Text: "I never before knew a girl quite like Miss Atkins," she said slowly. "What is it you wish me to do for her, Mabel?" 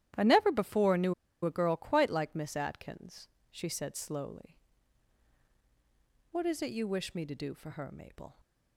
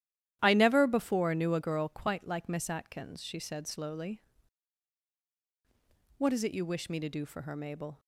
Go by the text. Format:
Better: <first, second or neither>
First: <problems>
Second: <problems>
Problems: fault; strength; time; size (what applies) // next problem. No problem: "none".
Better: second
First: starts louder than the rest; strong; until 1.4 s; 12 dB // pauses between "knew" and "a"; slight; at 1.1 s; 0.31 s long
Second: starts louder than the rest; strong; until 1.4 s; 12 dB